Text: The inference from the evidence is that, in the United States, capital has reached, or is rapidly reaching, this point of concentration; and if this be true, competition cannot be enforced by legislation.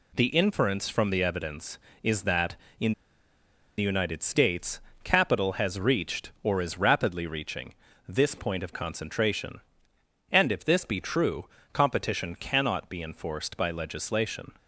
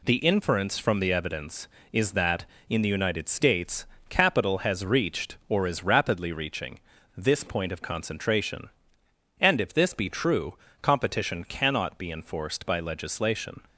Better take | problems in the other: second | pauses between "in" and "the"; noticeable; at 2.9 s; 0.86 s long

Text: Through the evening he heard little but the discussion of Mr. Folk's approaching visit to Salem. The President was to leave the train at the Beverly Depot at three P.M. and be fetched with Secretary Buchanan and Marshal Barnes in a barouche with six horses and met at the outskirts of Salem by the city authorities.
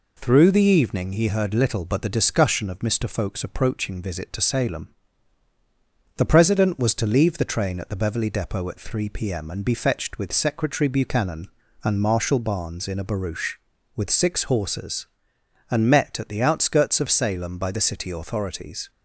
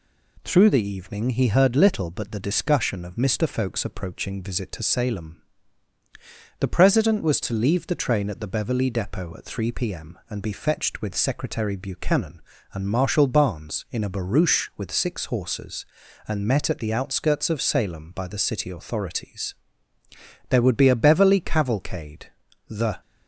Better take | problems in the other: first | goes on to say "There would be a Beverly cavalcade the"; strong; from 20.4 s on; 2.5 s long

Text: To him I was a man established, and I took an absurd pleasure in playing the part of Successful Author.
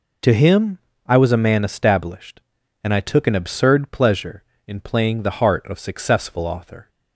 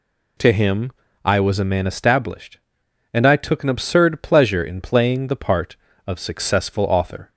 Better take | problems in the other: second | pauses between "him" and "I"; slight; at 0.7 s; 0.28 s long; slight in the second // says "heart" for "part"; at 5.3 s

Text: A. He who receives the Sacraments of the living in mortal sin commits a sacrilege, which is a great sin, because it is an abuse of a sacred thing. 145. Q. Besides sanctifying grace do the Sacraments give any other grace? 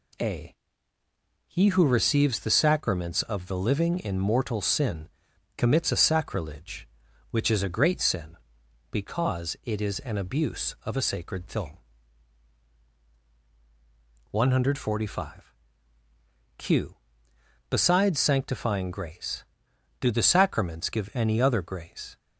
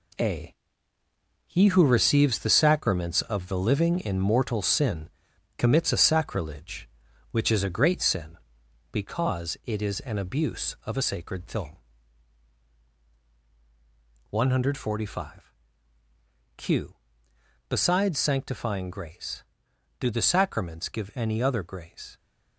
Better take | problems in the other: first | gets quieter; throughout; 7 dB // pauses between "sin" and "commits"; noticeable; at 5.0 s; 0.48 s long; noticeable in the first

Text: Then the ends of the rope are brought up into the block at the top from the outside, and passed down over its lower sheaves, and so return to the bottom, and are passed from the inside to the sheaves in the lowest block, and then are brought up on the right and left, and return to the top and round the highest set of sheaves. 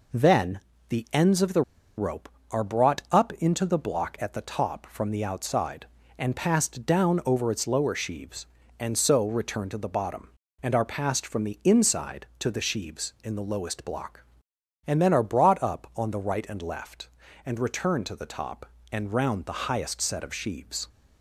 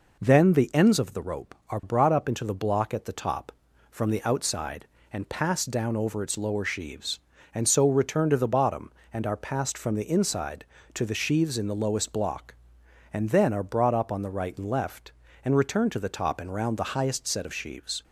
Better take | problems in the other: second | pauses between "Then" and "the"; slight; at 0.5 s; 0.30 s long // pauses between "the" and "rope"; at 1.6 s; 0.36 s long

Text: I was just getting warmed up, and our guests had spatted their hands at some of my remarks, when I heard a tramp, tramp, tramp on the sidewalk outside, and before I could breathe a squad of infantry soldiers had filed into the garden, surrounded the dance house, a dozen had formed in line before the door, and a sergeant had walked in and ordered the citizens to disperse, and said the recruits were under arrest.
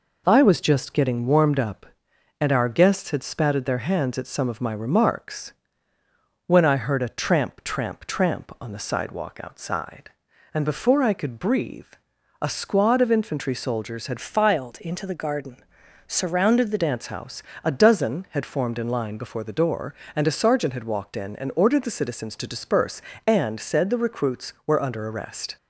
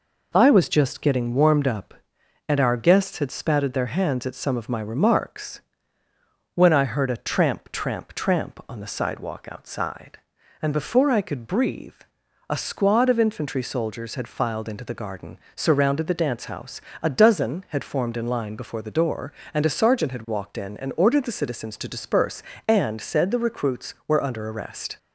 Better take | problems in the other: second | pauses between "breathe" and "a"; noticeable; at 11.8 s; 0.56 s long; noticeable in the second // changes voice from "filed" to "the"; from 14.1 to 16.7 s; 2.6 s long

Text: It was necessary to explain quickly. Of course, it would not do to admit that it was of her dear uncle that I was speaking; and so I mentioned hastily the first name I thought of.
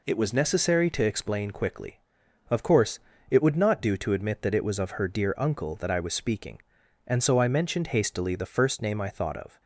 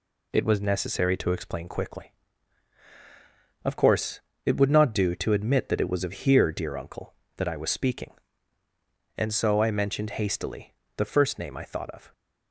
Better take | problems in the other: first | says "here" for "her"; at 6.1 s // pauses between "hastily" and "the"; slight; at 10.7 s; 0.26 s long

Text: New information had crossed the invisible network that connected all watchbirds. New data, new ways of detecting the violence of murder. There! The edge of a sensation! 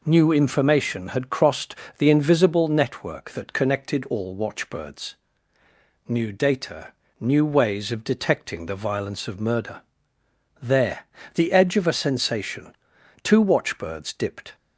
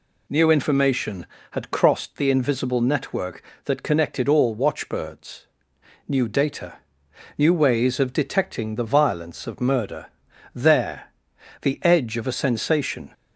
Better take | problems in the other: second | pauses between "crossed" and "the"; slight; at 1.7 s; 0.22 s long // goes on to say "Two watchbirds dipped"; from 13.2 s on; 1.3 s long

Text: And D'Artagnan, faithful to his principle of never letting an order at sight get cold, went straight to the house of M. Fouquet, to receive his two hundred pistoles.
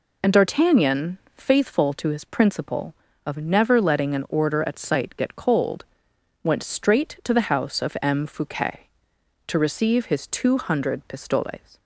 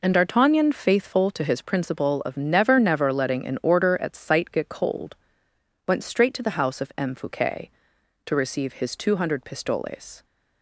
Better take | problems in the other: first | says "never" twice; at 2.7 s

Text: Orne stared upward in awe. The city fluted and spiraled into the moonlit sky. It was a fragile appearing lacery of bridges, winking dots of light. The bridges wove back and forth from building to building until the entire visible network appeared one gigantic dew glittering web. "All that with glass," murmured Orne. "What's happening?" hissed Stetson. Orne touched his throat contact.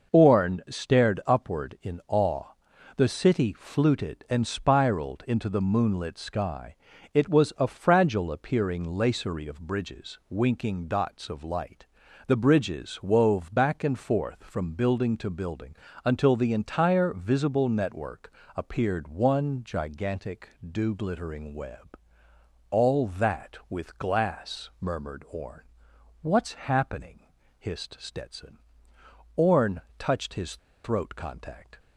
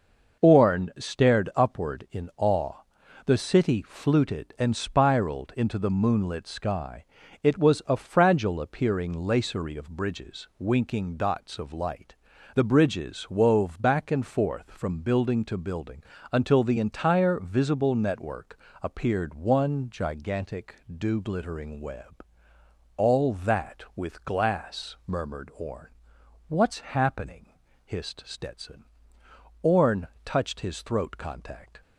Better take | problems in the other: second | pauses between "building" and "until"; slight; at 15.7 s; 0.30 s long; slight in the second // pauses between "network" and "appeared"; slight; at 18.3 s; 0.24 s long; slight in the second // pauses between "gigantic" and "dew"; slight; at 20.4 s; 0.18 s long; slight in the second // pauses between "Orne" and "touched"; slight; at 29.8 s; 0.16 s long; slight in the second // pauses between "his" and "throat"; slight; at 30.5 s; 0.27 s long

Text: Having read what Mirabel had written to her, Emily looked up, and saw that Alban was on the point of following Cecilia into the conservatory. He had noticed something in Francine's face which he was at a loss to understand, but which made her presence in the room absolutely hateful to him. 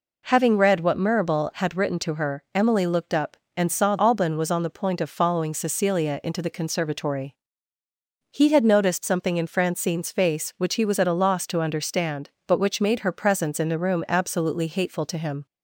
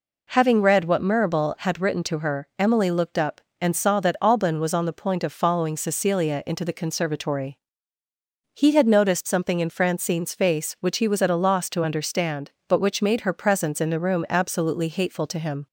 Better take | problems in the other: second | skips "that"; at 3.9 s

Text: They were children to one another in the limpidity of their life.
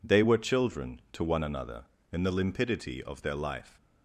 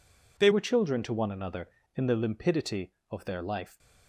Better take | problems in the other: first | changes voice at "were"; from 0.5 s on; 3.2 s long

